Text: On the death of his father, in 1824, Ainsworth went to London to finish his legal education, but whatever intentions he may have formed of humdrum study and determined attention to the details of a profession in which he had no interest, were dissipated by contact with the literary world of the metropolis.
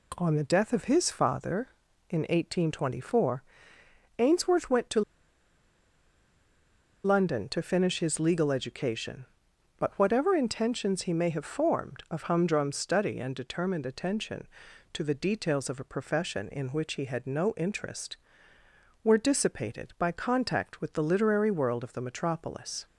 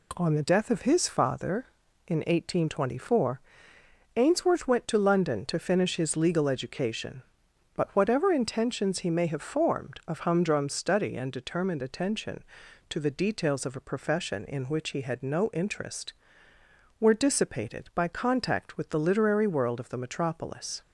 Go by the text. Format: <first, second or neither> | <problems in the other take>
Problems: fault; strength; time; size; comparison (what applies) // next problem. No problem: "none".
second | pauses between "to" and "London"; strong; at 5.0 s; 2.0 s long